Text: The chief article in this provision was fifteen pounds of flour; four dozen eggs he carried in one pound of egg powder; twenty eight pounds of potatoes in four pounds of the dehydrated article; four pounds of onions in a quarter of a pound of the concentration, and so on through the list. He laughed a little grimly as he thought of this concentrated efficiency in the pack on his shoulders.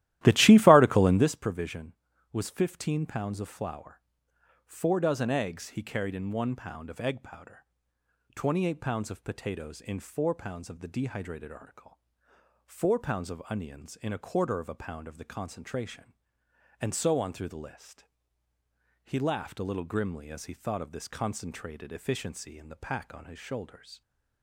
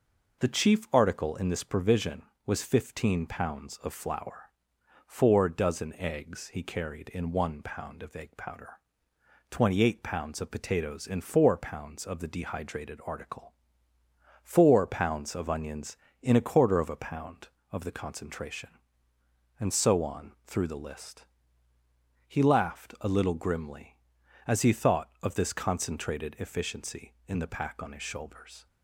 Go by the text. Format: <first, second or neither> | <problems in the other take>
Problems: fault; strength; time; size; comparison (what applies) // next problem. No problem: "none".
second | starts louder than the rest; strong; until 1.3 s; 14.5 dB